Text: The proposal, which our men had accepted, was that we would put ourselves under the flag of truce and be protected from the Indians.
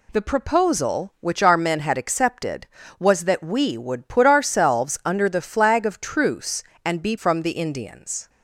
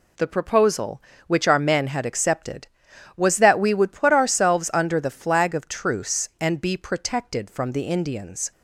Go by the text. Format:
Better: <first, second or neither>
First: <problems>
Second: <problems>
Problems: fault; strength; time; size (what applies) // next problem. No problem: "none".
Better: second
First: skips "protected"; at 7.1 s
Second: none